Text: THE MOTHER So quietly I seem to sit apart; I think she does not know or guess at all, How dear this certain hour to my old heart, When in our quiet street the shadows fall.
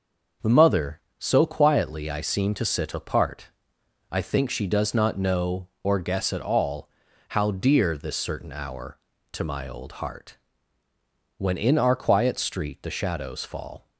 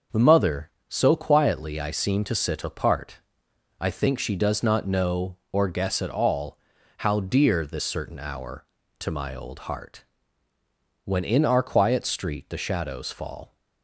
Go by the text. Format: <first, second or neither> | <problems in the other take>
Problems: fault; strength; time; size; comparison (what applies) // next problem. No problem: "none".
neither | starts louder than the rest; noticeable; the same in both